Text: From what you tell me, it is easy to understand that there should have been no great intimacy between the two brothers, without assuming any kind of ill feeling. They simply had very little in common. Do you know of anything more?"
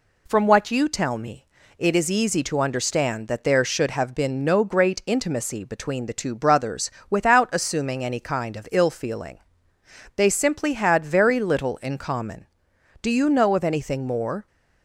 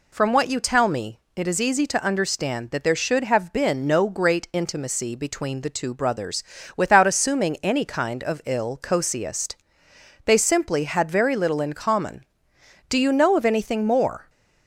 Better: first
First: none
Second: says "cosiest" for "feeling"; at 8.7 s

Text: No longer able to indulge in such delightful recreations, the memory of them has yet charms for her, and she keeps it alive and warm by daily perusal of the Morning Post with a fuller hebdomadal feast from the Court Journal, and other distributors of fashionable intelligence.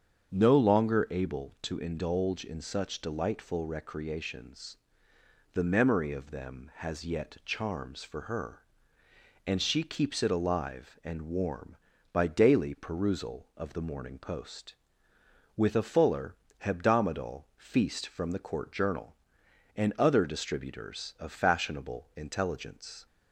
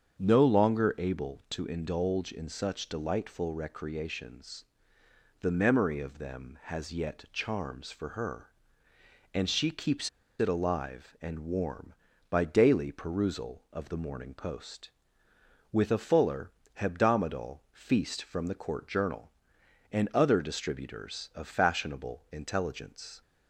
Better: first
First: starts louder than the rest; strong; until 1.3 s; 7.5 dB // pauses between "fuller" and "hebdomadal"; slight; at 16.3 s; 0.24 s long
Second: starts louder than the rest; strong; until 1.2 s; 7.5 dB // pauses between "keeps" and "it"; slight; at 10.0 s; 0.29 s long // pauses between "fuller" and "hebdomadal"; slight; at 16.5 s; 0.24 s long

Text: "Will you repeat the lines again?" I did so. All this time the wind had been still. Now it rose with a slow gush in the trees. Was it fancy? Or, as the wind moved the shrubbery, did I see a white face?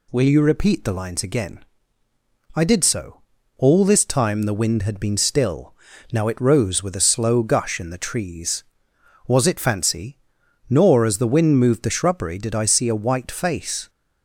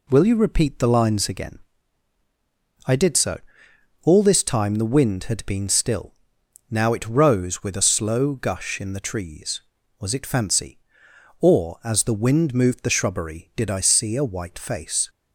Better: second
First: says "Nor" for "Or"; at 10.6 s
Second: none

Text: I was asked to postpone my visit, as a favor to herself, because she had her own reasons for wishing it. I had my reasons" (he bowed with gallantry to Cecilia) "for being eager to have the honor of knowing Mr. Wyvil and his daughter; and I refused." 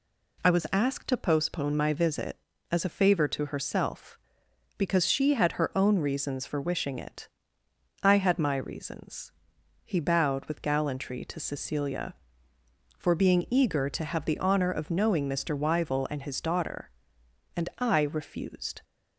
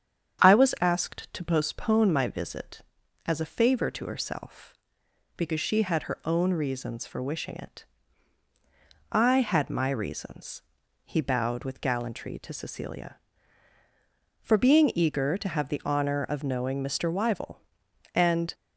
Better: first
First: none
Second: starts louder than the rest; strong; until 1.5 s; 8 dB // stops before "his daughter and I refused"; at 18.5 s

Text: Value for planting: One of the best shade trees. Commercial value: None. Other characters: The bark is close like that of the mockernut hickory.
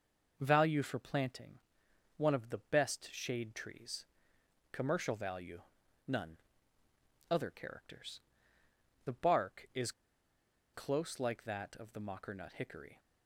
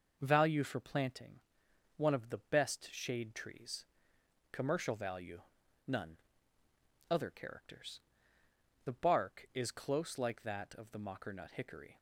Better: second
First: pauses between "is" and "close"; noticeable; at 9.9 s; 0.83 s long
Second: none

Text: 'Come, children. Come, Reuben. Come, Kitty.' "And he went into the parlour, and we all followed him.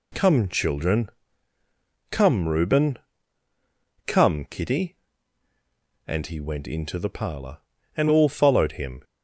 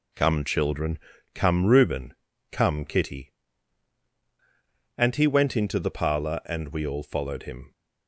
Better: second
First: skips "we"; at 8.0 s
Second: none

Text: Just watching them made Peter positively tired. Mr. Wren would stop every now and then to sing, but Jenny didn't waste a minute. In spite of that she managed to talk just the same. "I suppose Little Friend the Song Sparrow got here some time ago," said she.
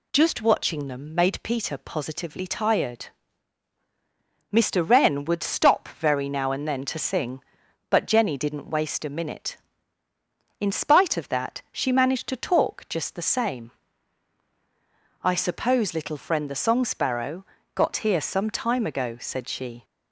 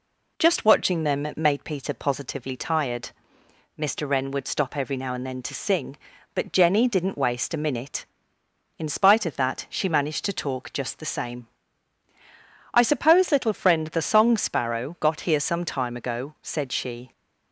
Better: second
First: says "very" for "every"; at 5.8 s // pauses between "Sparrow" and "got"; slight; at 17.4 s; 0.32 s long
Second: none

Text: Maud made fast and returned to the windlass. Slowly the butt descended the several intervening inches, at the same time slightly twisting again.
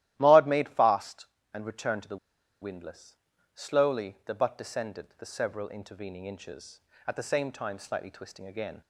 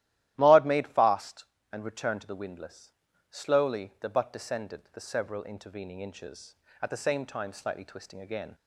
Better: second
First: starts louder than the rest; strong; until 1.1 s; 13.5 dB // pauses between "the" and "windlass"; at 2.1 s; 0.45 s long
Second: starts louder than the rest; strong; until 1.3 s; 13.5 dB

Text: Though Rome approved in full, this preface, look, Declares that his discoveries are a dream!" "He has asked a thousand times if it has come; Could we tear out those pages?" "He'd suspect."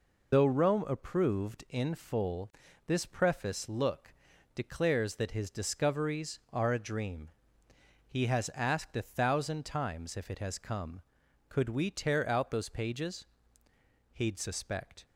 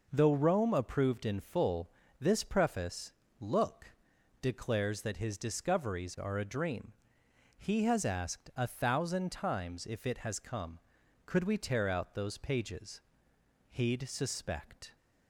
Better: second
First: loses the start of "Though"; at 0.3 s; 80 ms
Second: none

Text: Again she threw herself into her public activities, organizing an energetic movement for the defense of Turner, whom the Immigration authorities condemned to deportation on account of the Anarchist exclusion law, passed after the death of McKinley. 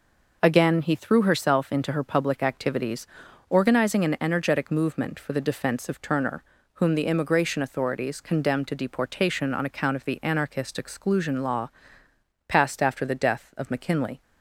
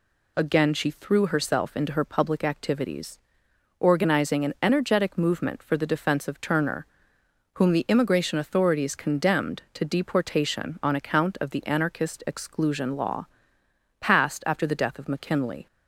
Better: second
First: says "he" for "she"; at 0.8 s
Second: none

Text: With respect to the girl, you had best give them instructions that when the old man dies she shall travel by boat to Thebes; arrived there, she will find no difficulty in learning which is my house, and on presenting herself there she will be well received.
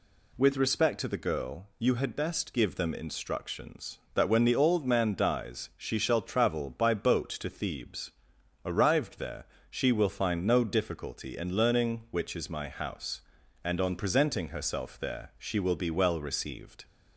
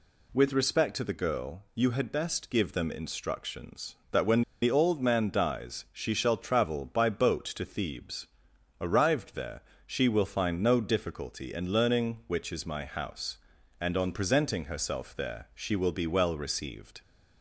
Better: first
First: none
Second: pauses between "when" and "the"; slight; at 4.4 s; 0.19 s long

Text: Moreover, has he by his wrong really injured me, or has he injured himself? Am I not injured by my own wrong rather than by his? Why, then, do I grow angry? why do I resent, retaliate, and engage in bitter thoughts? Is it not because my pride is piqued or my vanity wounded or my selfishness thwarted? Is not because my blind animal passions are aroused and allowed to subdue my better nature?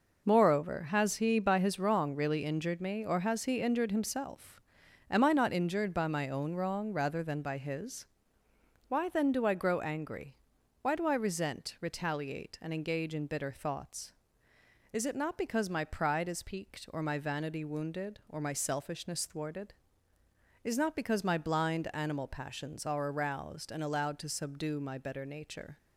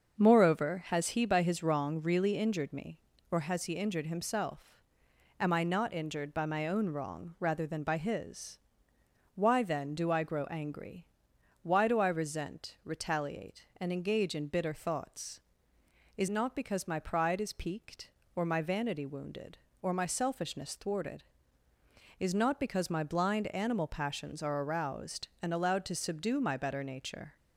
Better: first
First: none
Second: starts louder than the rest; until 1.2 s; 6.5 dB // skips "it"; at 16.2 s

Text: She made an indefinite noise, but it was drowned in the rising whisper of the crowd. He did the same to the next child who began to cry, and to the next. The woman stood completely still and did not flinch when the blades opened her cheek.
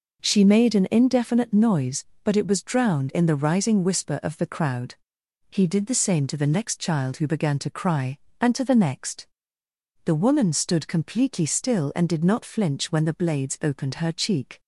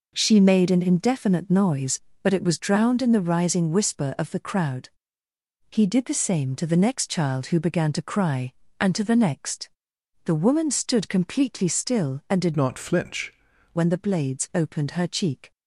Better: first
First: none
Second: changes voice from "not" to "flinch"; from 12.5 to 13.3 s; 0.8 s long

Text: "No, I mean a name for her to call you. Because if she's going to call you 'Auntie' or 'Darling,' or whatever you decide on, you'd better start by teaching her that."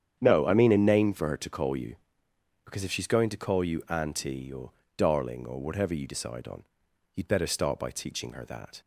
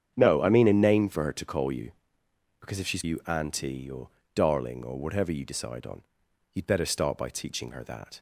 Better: first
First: starts louder than the rest; strong; until 1.2 s; 8.5 dB // pauses between "or" and "Darling"; slight; at 4.7 s; 0.26 s long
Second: starts louder than the rest; strong; until 1.1 s; 8.5 dB // skips "going to call"; at 3.0 s // pauses between "or" and "Darling"; slight; at 4.0 s; 0.26 s long

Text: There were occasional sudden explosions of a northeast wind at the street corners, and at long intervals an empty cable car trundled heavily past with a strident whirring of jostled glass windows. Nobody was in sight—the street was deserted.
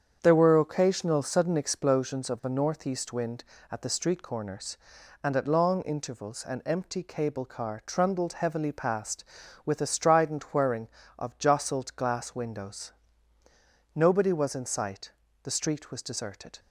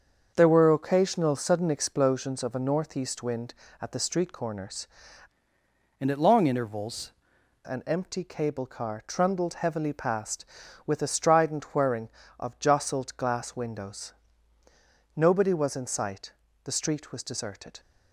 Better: first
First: starts louder than the rest; strong; until 1.2 s; 7.5 dB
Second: starts louder than the rest; until 1.3 s; 6.5 dB // changes voice from "and" to "intervals"; from 6.0 to 7.1 s; 1.1 s long

